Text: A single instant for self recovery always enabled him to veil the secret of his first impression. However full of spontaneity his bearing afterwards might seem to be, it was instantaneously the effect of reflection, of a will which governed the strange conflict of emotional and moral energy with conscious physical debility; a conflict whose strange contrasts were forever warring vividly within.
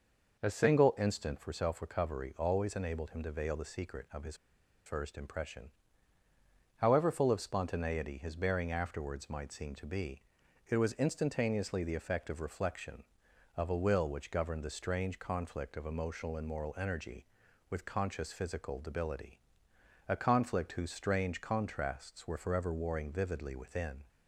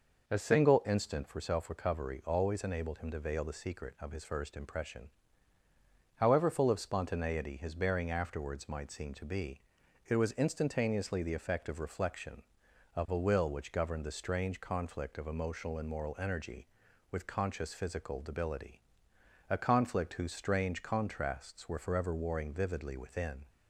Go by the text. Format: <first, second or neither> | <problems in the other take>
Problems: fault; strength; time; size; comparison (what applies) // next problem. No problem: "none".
second | pauses between "his" and "first"; noticeable; at 4.3 s; 0.50 s long